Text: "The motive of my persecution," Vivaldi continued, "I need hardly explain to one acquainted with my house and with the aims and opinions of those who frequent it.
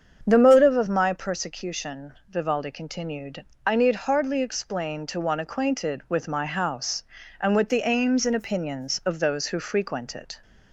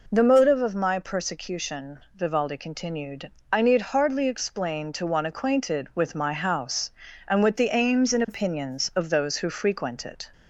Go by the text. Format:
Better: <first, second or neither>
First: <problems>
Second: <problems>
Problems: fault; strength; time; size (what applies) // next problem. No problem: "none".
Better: second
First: starts louder than the rest; strong; until 1.3 s; 7.5 dB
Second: none